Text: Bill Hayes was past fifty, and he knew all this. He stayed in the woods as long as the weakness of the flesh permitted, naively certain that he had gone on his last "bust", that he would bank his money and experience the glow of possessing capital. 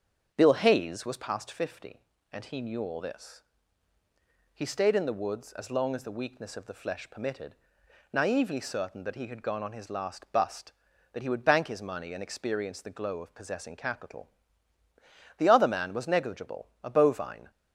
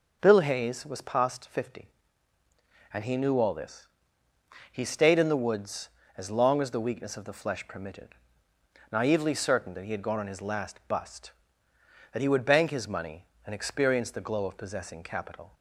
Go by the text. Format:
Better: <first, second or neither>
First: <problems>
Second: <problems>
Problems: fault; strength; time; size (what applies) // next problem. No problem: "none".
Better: second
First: starts louder than the rest; until 1.3 s; 6.5 dB // goes on to say "The other man was negligible a bovine"; strong; from 15.3 s on; 2.1 s long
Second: none